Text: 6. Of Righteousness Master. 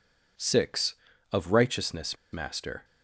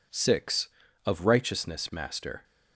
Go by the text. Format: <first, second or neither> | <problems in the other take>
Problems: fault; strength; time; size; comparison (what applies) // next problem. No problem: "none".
second | pauses between "Righteousness" and "Master"; slight; at 2.1 s; 0.18 s long